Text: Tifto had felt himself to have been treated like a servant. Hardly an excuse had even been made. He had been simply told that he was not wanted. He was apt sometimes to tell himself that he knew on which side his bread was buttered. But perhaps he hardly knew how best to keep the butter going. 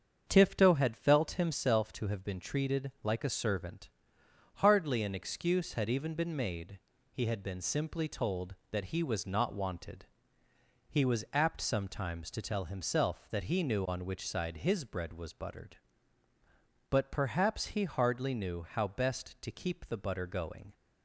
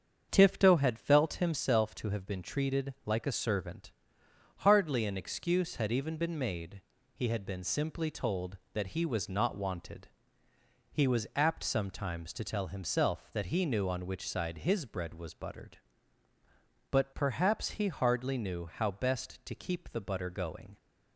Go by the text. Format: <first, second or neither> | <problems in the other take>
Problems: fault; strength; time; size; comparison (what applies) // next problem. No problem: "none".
neither | starts louder than the rest; strong; the same in both